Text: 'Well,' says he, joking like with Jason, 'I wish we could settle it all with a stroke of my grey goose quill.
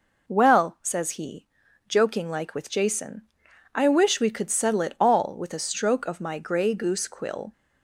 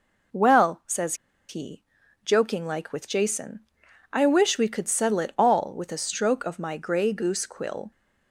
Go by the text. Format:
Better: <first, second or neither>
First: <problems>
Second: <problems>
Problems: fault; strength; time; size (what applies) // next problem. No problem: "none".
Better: first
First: none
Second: pauses between "says" and "he"; slight; at 1.1 s; 0.34 s long